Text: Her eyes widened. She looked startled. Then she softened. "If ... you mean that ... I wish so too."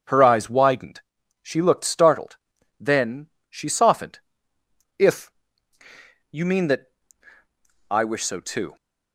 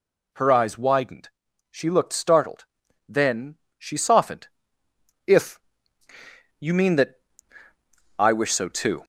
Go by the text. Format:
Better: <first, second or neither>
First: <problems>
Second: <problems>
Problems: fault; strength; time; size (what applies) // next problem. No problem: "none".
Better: first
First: pauses between "Then" and "she"; slight; at 3.2 s; 0.22 s long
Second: gets louder; slight; throughout; 2.5 dB // pauses between "Then" and "she"; slight; at 3.5 s; 0.22 s long